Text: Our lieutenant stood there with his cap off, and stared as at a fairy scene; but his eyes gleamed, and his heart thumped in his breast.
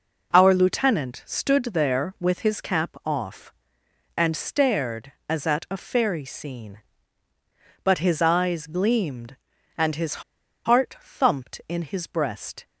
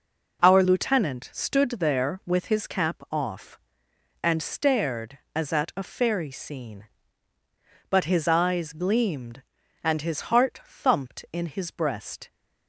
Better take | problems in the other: second | pauses between "his" and "heart"; at 10.2 s; 0.42 s long

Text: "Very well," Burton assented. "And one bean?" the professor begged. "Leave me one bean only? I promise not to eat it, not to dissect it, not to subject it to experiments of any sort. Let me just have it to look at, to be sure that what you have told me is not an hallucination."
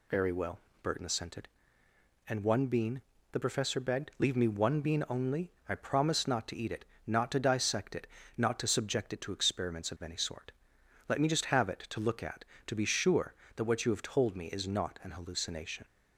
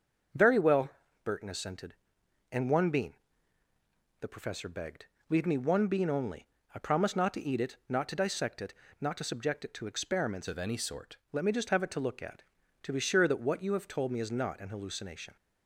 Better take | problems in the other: first | starts louder than the rest; until 1.7 s; 6.5 dB // changes voice from "of" to "sort"; from 10.4 to 11.1 s; 0.7 s long

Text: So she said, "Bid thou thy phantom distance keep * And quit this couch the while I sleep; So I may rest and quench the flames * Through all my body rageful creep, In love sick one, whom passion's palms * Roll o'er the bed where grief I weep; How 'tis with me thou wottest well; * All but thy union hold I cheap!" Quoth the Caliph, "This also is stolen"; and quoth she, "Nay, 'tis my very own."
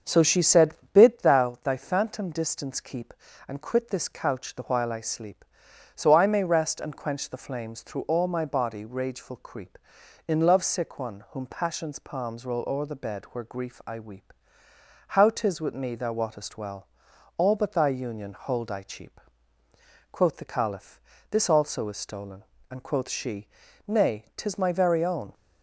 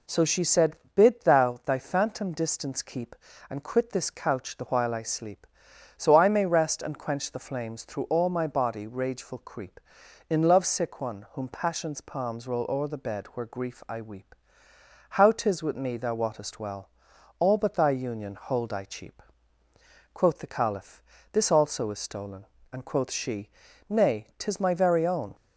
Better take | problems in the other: second | starts louder than the rest; until 1.3 s; 6.5 dB

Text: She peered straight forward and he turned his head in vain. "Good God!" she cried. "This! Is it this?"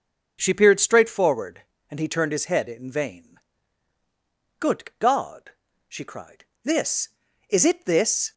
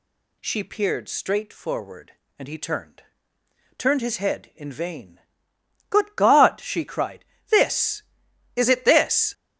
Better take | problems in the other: first | says "turned" twice; at 3.7 s

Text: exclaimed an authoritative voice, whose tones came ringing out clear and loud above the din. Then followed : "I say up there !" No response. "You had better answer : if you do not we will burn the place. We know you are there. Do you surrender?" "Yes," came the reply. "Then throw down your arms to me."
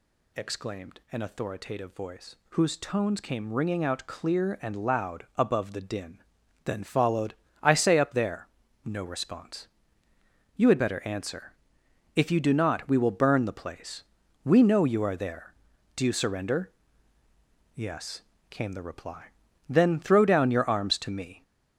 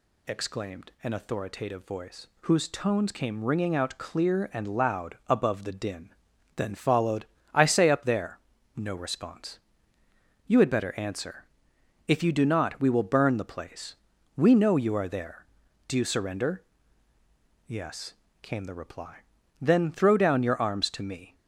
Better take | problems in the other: second | gets louder; noticeable; throughout; 5 dB

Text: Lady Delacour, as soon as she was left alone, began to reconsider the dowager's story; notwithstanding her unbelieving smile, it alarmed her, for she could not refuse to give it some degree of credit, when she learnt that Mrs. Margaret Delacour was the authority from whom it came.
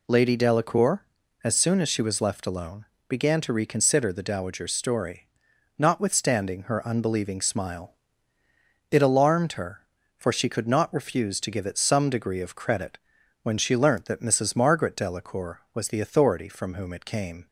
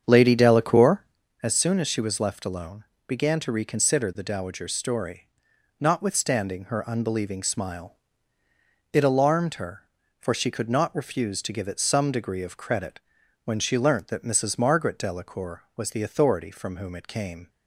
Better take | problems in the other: first | starts louder than the rest; strong; until 1.3 s; 7.5 dB

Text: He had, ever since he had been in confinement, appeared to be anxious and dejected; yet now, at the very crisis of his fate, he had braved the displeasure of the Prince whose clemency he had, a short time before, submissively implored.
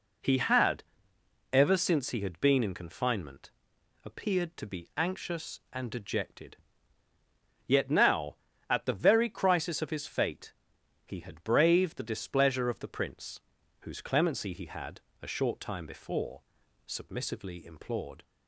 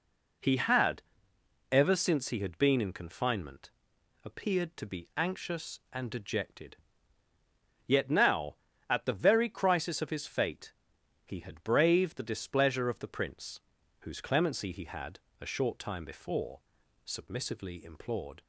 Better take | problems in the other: neither | pauses between "Prince" and "whose"; the same in both

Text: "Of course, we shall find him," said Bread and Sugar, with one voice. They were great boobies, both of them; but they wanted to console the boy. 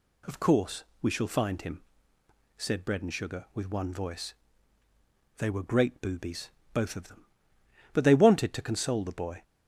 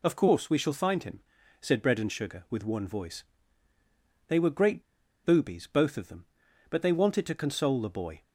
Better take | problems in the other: first | pauses between "great" and "boobies"; at 4.8 s; 0.43 s long

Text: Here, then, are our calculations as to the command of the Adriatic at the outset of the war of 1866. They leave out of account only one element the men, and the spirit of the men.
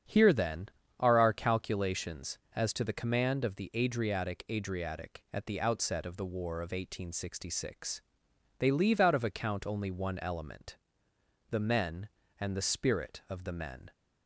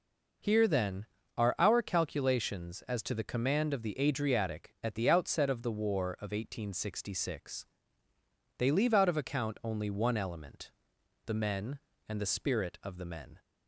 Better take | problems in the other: second | starts louder than the rest; strong; until 1.4 s; 8 dB // says "Adriatic" twice; at 4.4 s // pauses between "element" and "the"; noticeable; at 10.7 s; 0.72 s long; noticeable in the second

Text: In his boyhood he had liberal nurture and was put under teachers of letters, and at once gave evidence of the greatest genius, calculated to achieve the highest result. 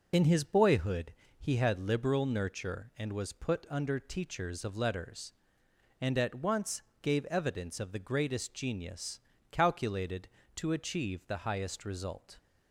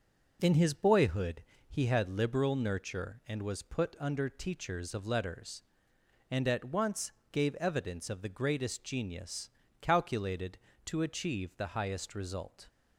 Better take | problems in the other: second | loses the start of "In"; at 0.1 s; 35 ms // pauses between "boyhood" and "he"; slight; at 1.1 s; 0.26 s long; slight in the second // pauses between "once" and "gave"; slight; at 6.8 s; 0.20 s long; slight in the second

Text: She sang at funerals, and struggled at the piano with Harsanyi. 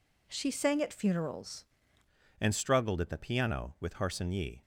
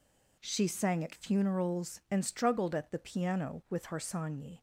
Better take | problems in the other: second | changes voice at "and"; from 2.3 s on; 2.3 s long

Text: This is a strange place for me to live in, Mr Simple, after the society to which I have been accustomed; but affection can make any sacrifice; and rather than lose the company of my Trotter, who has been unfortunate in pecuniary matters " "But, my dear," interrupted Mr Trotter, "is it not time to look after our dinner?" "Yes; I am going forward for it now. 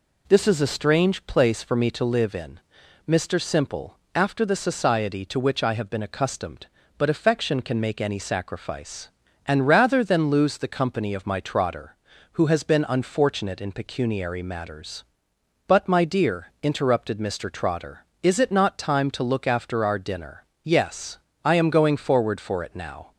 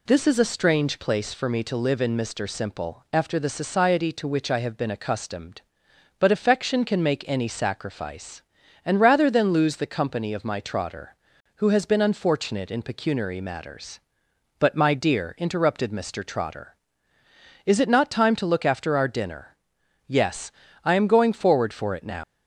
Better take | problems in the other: first | leaves "now" unfinished; at 22.2 s; 120 ms

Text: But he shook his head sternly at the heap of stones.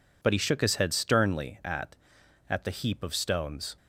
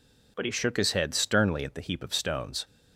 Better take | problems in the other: second | says "at" twice; at 2.4 s

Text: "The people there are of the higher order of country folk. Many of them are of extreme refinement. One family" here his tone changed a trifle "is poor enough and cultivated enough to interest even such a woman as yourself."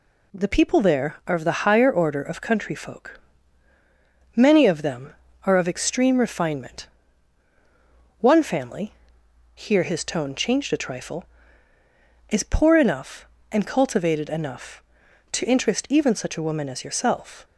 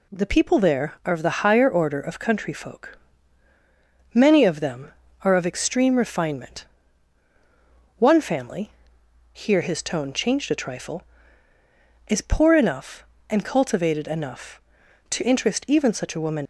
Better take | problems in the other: first | pauses between "family" and "here"; noticeable; at 8.7 s; 0.62 s long; noticeable in the first // stops before "as yourself"; at 16.4 s

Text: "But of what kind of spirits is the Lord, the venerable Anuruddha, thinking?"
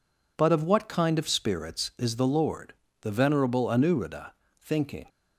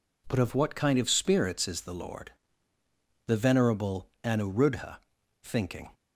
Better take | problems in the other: neither | none

